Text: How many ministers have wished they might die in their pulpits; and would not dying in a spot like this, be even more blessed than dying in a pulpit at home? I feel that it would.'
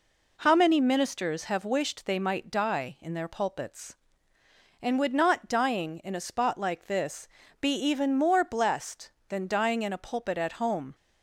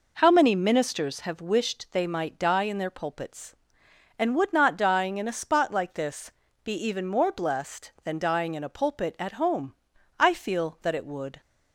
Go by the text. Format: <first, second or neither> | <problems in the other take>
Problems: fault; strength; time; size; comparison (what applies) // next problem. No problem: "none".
second | stops before "I feel that it would"; at 10.9 s